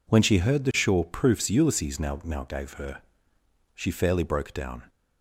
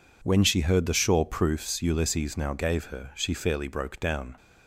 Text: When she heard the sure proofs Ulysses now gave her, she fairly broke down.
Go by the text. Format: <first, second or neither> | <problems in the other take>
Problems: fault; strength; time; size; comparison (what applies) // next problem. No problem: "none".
second | says "now" twice; at 2.2 s